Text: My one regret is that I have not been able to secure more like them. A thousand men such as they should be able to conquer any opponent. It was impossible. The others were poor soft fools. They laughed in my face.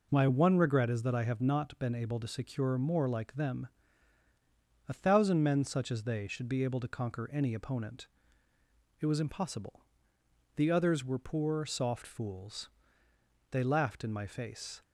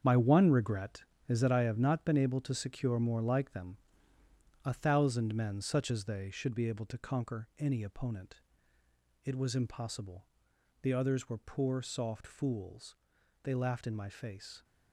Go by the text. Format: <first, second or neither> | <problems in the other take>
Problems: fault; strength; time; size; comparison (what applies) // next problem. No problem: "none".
first | gets quieter; strong; throughout; 10 dB